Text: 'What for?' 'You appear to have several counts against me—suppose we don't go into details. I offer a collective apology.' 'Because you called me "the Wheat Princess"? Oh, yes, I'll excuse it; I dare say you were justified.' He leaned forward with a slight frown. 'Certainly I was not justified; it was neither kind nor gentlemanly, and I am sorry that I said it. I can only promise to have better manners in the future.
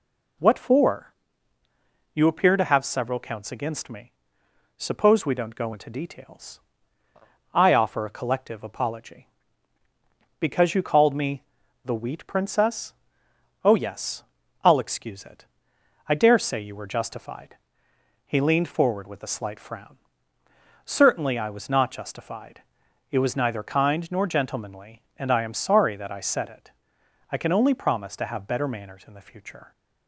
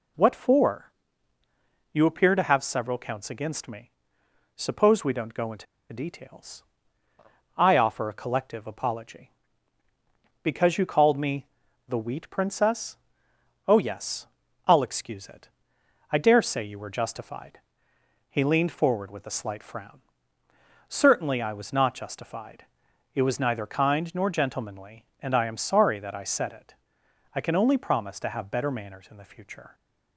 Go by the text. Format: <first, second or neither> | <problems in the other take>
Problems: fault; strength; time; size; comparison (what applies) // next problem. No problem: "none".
first | pauses between "into" and "details"; slight; at 5.6 s; 0.26 s long // pauses between "me" and "the"; at 11.4 s; 0.40 s long; also in the first